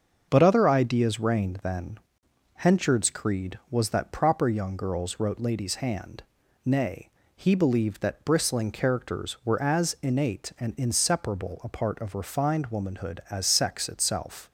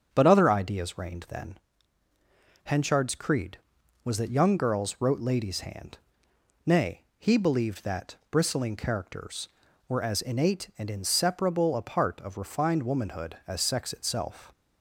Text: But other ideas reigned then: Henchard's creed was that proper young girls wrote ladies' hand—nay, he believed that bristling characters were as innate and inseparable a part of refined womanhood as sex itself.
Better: first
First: starts louder than the rest; until 1.3 s; 6.5 dB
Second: starts louder than the rest; strong; until 1.1 s; 7.5 dB // skips "proper"; at 4.3 s // pauses between "that" and "bristling"; slight; at 8.1 s; 0.16 s long

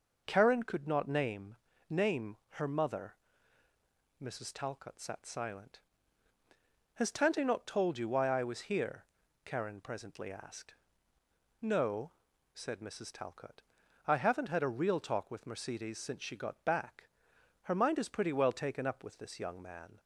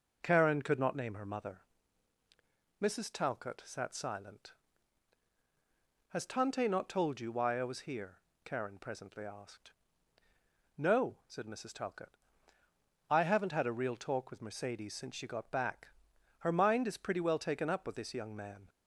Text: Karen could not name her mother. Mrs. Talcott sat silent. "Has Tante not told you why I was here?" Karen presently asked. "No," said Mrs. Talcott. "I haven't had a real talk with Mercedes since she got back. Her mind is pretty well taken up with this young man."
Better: second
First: says "name" twice; at 1.8 s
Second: none

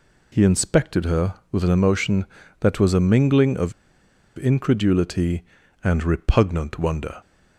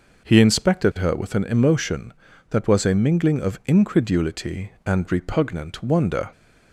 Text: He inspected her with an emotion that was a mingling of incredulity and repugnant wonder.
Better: second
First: pauses between "of" and "incredulity"; noticeable; at 3.7 s; 0.65 s long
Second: none

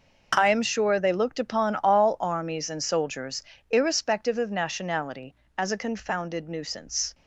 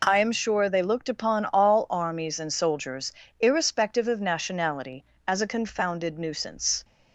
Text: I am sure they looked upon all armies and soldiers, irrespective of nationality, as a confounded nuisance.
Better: second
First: gets quieter; strong; throughout; 12.5 dB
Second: none

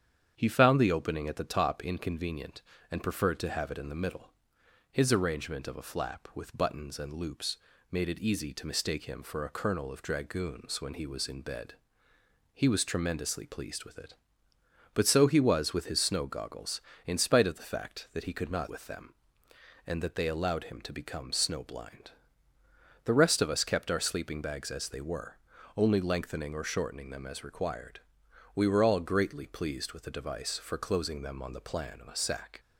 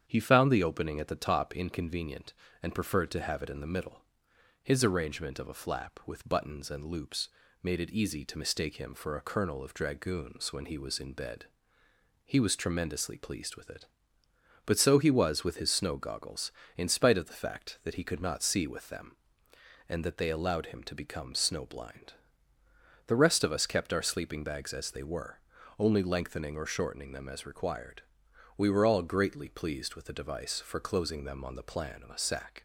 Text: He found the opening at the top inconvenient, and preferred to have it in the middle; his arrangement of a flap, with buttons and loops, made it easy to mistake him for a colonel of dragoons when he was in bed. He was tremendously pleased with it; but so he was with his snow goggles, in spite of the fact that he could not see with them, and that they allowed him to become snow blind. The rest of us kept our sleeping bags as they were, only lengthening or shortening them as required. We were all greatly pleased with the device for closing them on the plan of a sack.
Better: second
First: starts louder than the rest; strong; until 1.3 s; 8.5 dB // skips "see"; at 18.6 s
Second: starts louder than the rest; strong; until 1.0 s; 8.5 dB

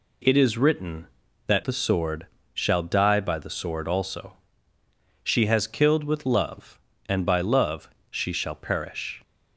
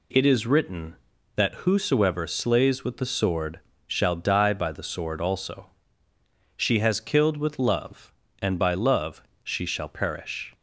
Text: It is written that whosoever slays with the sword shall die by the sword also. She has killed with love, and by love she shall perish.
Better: second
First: skips "whosoever slays with"; at 1.6 s // pauses between "sword" and "shall"; slight; at 2.2 s; 0.26 s long // pauses between "love" and "she"; slight; at 7.9 s; 0.18 s long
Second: pauses between "sword" and "shall"; slight; at 3.6 s; 0.26 s long // pauses between "love" and "she"; slight; at 9.2 s; 0.18 s long

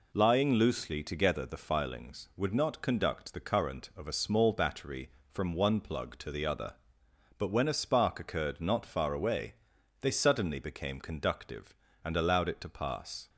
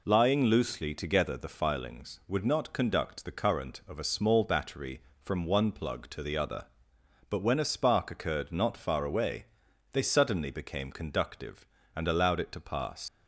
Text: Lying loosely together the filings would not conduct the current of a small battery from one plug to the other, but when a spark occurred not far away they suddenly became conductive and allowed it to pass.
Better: first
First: pauses between "away" and "they"; noticeable; at 9.5 s; 0.48 s long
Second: pauses between "away" and "they"; noticeable; at 9.4 s; 0.48 s long // leaves "pass" unfinished; at 13.0 s; 120 ms

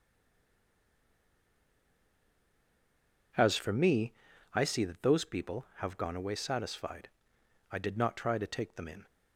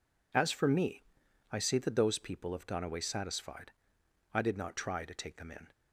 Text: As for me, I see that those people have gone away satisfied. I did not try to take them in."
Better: second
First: stays silent before the first word; strong; until 3.3 s; 3.3 s long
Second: none

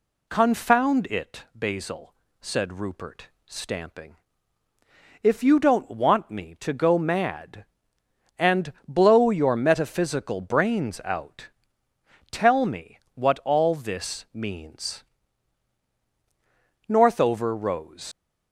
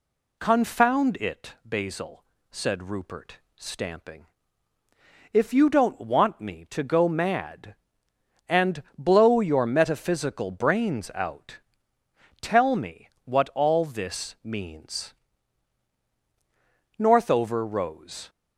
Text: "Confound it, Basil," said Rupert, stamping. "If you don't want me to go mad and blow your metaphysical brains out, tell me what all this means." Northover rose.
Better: second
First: pauses between "and" and "blow"; slight; at 8.7 s; 0.16 s long // pauses between "me" and "what"; slight; at 12.9 s; 0.16 s long // leaves "rose" unfinished; at 18.1 s; 75 ms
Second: pauses between "and" and "blow"; slight; at 8.8 s; 0.16 s long // pauses between "me" and "what"; slight; at 13.0 s; 0.16 s long

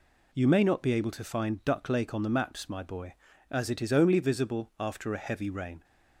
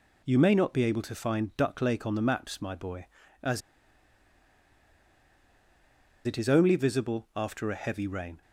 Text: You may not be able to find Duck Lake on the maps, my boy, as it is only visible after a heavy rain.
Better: first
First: none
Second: pauses between "as" and "it"; strong; at 3.6 s; 2.6 s long

